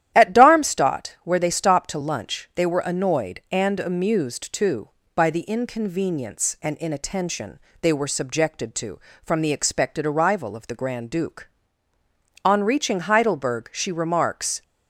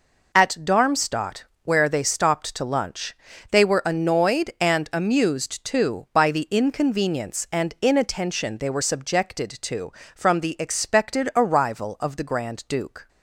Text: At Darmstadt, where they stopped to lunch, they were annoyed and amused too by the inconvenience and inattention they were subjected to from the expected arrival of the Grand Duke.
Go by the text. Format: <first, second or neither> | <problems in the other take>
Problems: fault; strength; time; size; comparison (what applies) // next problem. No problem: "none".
second | starts louder than the rest; strong; until 1.1 s; 11.5 dB // pauses between "inattention" and "they"; slight; at 7.5 s; 0.22 s long // goes on to say "On reaching Heidelberg she remarks"; strong; from 12.4 s on; 2.1 s long